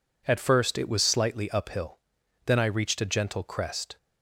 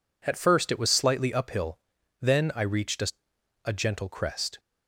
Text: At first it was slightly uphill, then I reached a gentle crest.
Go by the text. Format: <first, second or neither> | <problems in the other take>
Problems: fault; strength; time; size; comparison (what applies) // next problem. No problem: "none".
first | says "a" twice; at 3.6 s